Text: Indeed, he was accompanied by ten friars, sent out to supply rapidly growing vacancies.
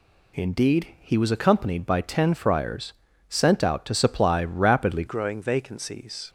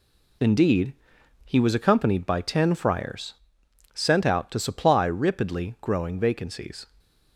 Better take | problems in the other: second | changes voice at "growing"; from 5.0 s on; 1.2 s long

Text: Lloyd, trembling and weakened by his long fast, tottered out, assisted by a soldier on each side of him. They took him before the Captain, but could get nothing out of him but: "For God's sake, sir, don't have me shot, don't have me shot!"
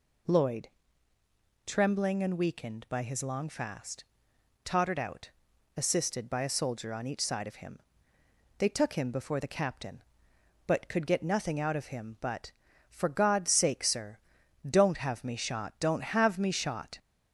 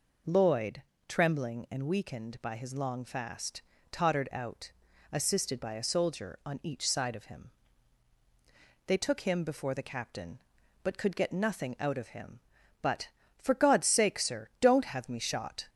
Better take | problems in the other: first | stops before "don't have me shot"; at 15.6 s

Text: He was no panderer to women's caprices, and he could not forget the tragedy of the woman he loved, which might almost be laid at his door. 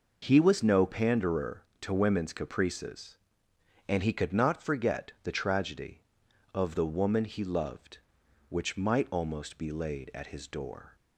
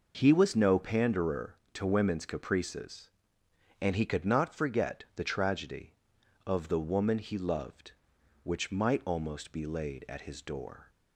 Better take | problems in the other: neither | none

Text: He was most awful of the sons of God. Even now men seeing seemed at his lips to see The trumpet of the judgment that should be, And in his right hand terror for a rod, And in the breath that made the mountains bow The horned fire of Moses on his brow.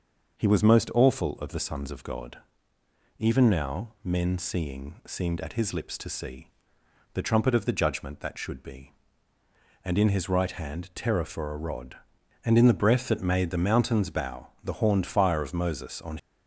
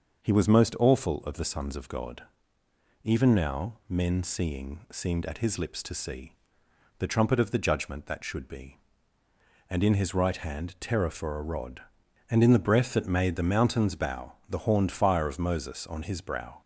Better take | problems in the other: second | starts louder than the rest; until 1.4 s; 6.5 dB; also in the second // pauses between "see" and "The"; noticeable; at 6.5 s; 0.64 s long; noticeable in the second // stops before "his brow"; at 16.1 s

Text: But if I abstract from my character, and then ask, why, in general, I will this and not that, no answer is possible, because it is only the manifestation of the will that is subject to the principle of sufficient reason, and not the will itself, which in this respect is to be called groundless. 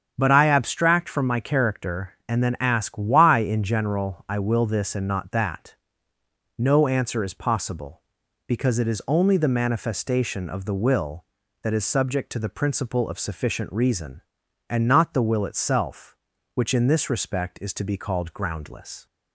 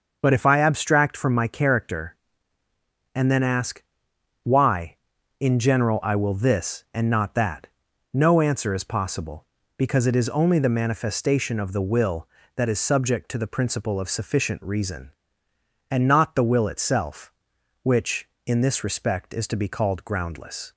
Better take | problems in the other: second | starts louder than the rest; strong; until 1.1 s; 8 dB; also in the second // skips "if"; at 0.3 s

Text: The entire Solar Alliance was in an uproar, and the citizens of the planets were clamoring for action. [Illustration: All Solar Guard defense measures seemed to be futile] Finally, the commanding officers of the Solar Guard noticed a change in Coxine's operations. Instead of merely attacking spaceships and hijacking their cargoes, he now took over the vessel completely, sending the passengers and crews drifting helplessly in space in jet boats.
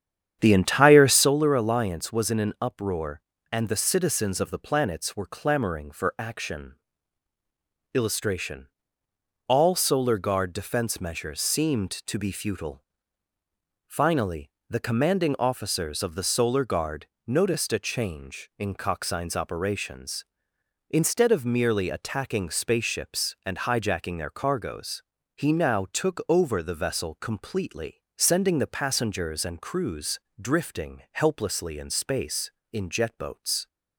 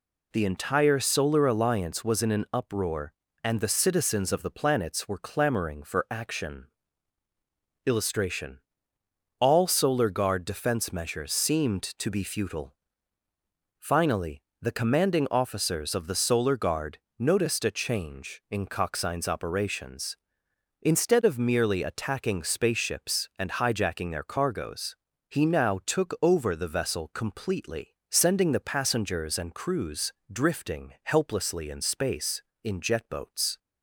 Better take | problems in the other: second | starts louder than the rest; strong; until 1.3 s; 9 dB // pauses between "futile" and "Finally"; at 12.8 s; 1.0 s long; also in the second // pauses between "Guard" and "noticed"; slight; at 17.0 s; 0.20 s long; slight in the second // pauses between "crews" and "drifting"; slight; at 30.1 s; 0.22 s long; slight in the second

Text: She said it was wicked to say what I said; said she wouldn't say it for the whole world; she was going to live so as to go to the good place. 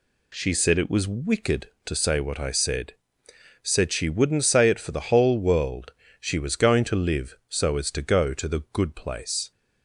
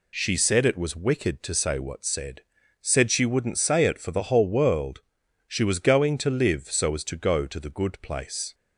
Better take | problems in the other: first | skips "I"; at 2.0 s

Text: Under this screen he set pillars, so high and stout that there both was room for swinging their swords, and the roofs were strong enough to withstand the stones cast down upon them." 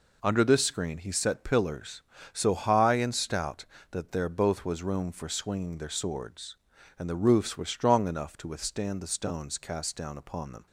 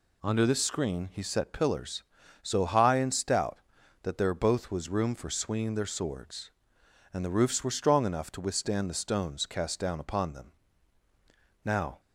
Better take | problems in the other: first | goes on to say "Now"; slight; from 11.6 s on; 0.36 s long

